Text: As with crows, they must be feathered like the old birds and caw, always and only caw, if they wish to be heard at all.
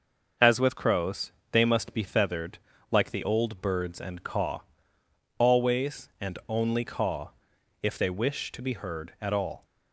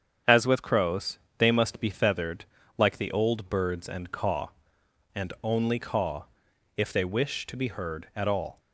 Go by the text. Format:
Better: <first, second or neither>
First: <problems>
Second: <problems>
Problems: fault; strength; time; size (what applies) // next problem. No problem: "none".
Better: first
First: pauses between "feathered" and "like"; slight; at 2.5 s; 0.34 s long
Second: starts louder than the rest; strong; until 1.4 s; 8 dB // pauses between "feathered" and "like"; slight; at 2.4 s; 0.34 s long // skips "always"; at 4.8 s